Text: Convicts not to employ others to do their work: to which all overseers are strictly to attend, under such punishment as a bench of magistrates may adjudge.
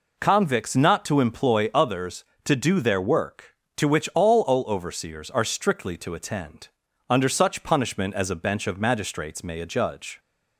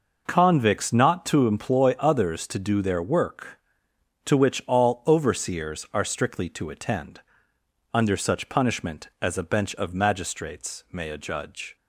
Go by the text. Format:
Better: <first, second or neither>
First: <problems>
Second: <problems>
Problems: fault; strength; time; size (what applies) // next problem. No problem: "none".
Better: second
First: says "all" twice; at 4.4 s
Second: none